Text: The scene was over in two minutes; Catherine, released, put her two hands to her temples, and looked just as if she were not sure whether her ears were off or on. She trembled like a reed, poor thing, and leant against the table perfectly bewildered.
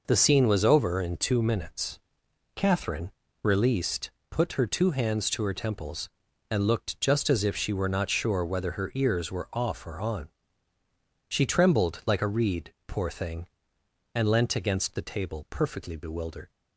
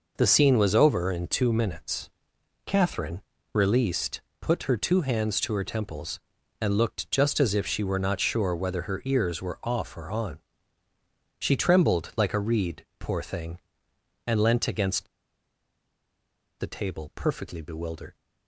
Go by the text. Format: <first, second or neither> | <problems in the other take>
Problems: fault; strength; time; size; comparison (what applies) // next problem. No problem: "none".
first | pauses between "against" and "the"; strong; at 15.0 s; 1.5 s long